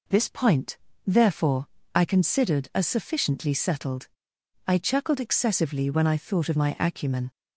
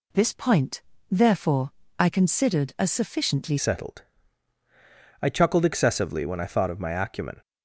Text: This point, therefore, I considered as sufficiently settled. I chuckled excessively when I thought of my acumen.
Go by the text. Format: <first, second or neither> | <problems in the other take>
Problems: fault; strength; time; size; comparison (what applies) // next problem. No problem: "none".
first | changes voice at "settled"; from 3.5 s on; 3.9 s long